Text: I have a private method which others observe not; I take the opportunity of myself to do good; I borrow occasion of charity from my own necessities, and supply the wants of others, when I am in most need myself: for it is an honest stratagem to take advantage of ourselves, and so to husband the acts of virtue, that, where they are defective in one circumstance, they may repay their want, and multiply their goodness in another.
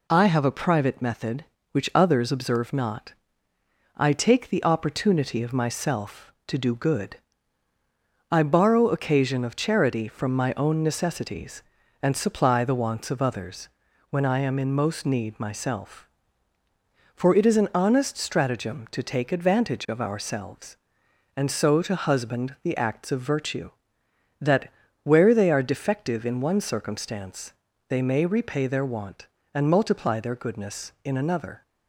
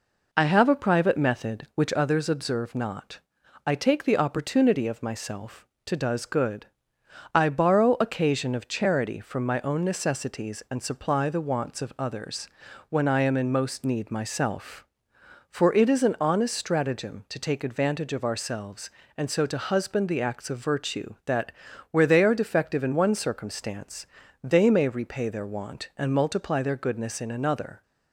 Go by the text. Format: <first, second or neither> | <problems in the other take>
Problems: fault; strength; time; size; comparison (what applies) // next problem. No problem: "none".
first | says "does" for "do"; at 5.9 s